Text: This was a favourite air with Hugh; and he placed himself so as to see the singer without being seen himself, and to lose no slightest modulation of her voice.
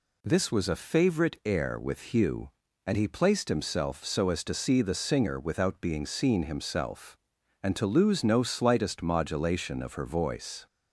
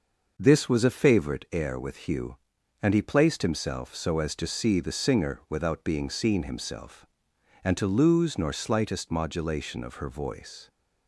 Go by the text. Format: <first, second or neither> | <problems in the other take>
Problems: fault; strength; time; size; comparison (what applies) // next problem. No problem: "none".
first | says "nor" for "no"; at 8.3 s